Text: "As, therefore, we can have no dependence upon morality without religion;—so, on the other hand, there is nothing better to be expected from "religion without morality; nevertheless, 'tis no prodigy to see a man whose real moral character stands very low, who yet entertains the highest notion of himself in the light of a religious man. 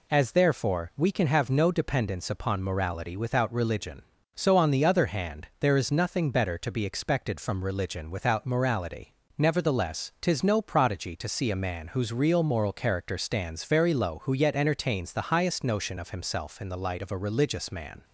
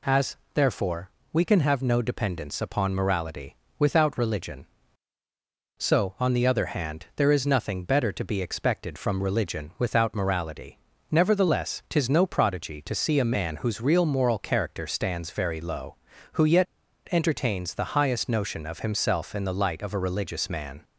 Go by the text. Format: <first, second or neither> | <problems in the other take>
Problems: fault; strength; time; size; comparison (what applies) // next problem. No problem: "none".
first | pauses between "morality" and "without"; slight; at 3.5 s; 0.22 s long // pauses between "yet" and "entertains"; at 16.6 s; 0.44 s long